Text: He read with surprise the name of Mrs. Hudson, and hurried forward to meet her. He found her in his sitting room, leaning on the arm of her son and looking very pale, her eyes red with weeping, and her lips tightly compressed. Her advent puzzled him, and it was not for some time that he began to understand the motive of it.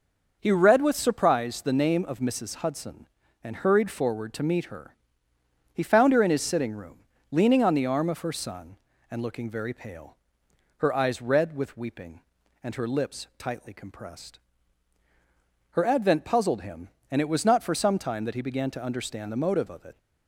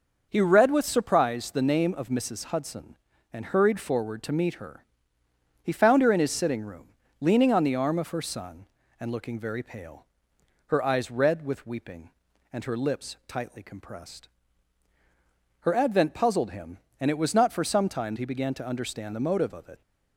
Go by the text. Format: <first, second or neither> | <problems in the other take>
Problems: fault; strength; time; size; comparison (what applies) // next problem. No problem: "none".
first | starts louder than the rest; noticeable; until 1.3 s; 6 dB; noticeable in the first // skips "that"; at 18.1 s